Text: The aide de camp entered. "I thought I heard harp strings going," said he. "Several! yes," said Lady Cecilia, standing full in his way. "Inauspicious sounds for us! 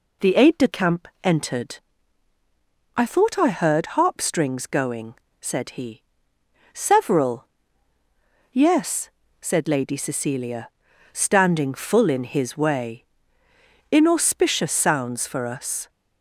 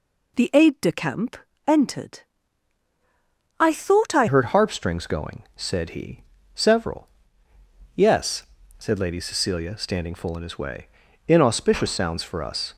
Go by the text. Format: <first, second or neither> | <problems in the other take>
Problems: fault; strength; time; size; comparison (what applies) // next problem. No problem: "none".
first | pauses between "camp" and "entered"; slight; at 1.3 s; 0.28 s long; slight in the first // changes voice at "heard"; from 4.2 s on; 8.5 s long